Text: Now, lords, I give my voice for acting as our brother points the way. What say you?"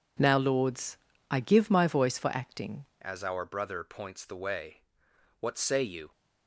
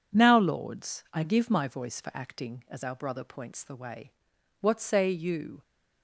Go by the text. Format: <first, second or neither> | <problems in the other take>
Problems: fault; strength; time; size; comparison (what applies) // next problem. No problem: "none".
second | changes voice at "as"; from 3.0 s on; 3.1 s long